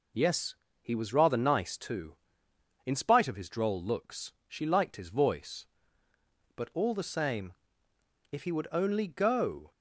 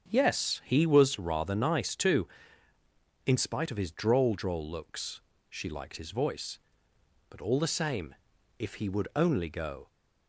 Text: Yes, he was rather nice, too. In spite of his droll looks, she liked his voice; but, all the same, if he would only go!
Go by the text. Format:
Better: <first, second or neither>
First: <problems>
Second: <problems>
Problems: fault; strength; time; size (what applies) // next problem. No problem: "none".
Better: first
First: none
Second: starts louder than the rest; strong; until 1.1 s; 7 dB // says "droll" twice; at 4.3 s